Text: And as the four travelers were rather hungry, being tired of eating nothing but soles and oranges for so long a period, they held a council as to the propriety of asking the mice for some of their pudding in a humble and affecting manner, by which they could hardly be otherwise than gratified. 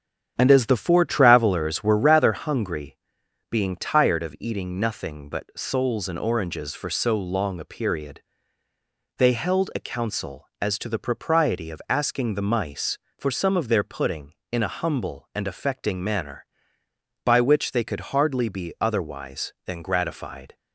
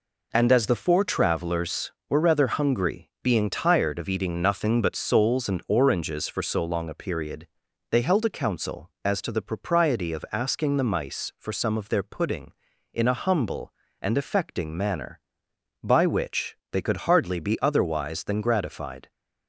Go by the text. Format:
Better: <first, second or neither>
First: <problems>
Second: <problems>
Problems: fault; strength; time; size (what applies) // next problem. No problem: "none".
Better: second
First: starts louder than the rest; strong; until 2.0 s; 8.5 dB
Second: none